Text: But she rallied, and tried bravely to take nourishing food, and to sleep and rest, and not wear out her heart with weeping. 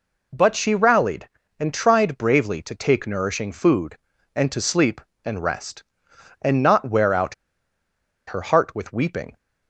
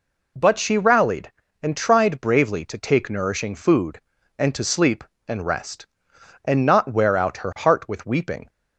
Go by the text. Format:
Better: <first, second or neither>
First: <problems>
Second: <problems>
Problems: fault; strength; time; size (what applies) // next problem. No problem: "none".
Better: second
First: pauses between "out" and "her"; noticeable; at 7.3 s; 0.93 s long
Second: none